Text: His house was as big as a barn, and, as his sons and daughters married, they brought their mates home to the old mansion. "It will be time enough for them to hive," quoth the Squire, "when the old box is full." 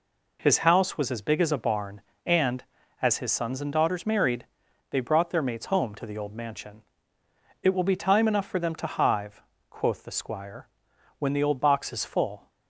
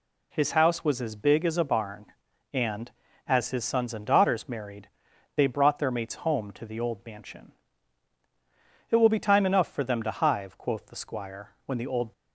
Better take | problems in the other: first | stops before "box is full"; at 12.1 s

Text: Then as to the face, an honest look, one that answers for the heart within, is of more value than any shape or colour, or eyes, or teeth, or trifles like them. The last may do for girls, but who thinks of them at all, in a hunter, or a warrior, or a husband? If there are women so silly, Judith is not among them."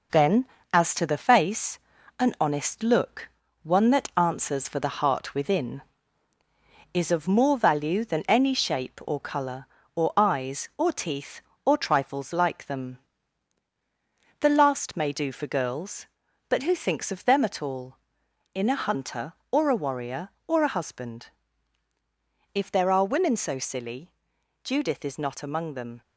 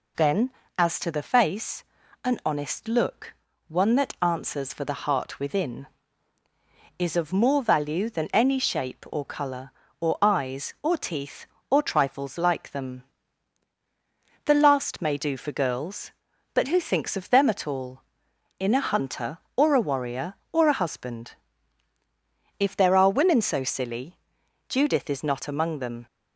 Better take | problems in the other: second | gets quieter; noticeable; throughout; 4.5 dB

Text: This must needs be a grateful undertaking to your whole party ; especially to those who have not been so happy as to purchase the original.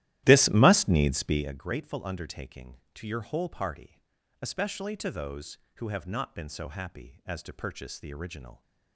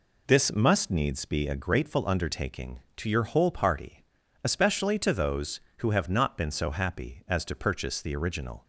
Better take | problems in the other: second | starts louder than the rest; strong; until 1.5 s; 14.5 dB

